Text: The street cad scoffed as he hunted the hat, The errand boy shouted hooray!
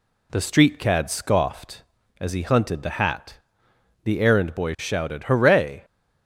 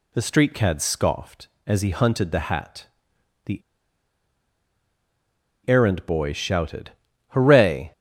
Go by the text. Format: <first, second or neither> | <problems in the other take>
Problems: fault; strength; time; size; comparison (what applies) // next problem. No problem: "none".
first | pauses between "The" and "errand"; strong; at 3.6 s; 2.0 s long // pauses between "shouted" and "hooray"; at 6.8 s; 0.38 s long